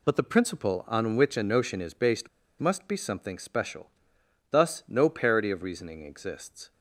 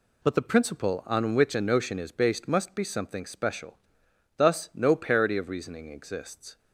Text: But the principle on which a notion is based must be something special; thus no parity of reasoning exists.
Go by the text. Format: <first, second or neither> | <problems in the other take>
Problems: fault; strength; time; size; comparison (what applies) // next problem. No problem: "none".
second | pauses between "based" and "must"; slight; at 2.2 s; 0.31 s long